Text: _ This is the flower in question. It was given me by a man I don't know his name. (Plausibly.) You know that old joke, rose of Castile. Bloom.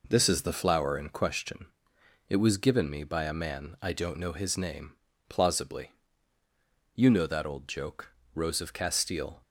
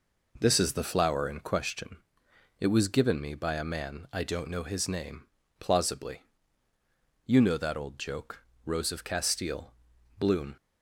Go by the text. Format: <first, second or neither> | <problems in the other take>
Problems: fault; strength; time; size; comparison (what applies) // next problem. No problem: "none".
second | stops before "Bloom"; at 9.4 s